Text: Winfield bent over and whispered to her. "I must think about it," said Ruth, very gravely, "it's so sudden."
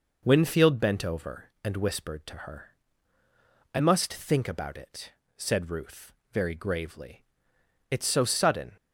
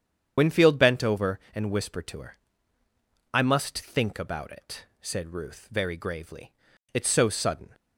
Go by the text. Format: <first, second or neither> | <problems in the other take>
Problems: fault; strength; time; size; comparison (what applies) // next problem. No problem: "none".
first | loses the start of "Winfield"; at 0.3 s; 65 ms // starts louder than the rest; strong; until 1.3 s; 8.5 dB